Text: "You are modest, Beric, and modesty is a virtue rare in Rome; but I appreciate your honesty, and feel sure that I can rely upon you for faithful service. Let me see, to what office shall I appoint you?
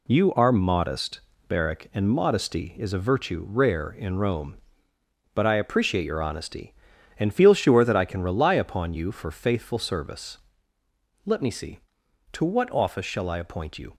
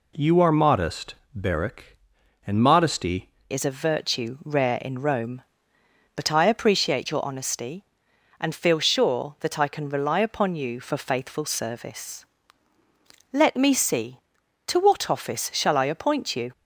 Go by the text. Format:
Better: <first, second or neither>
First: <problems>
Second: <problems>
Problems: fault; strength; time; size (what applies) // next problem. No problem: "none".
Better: first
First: none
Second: changes voice at "is"; from 3.5 s on; 13.0 s long